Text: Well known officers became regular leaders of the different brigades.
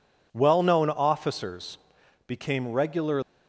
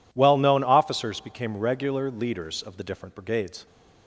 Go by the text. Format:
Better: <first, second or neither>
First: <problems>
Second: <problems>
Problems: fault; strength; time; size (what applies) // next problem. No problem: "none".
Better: second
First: pauses between "officers" and "became"; noticeable; at 1.7 s; 0.50 s long // stops before "leaders of the different brigades"; at 3.2 s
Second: none